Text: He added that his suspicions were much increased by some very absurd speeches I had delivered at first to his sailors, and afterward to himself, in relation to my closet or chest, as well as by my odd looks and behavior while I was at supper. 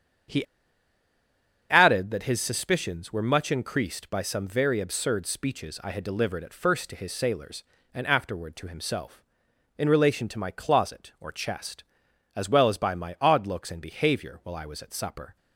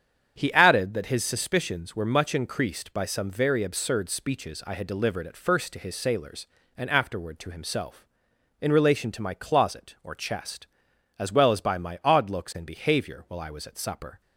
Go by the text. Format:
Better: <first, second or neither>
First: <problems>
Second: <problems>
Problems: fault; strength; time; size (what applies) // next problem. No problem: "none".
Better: second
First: starts louder than the rest; strong; until 2.5 s; 8 dB // pauses between "He" and "added"; strong; at 0.4 s; 1.2 s long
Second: starts louder than the rest; strong; until 1.3 s; 8 dB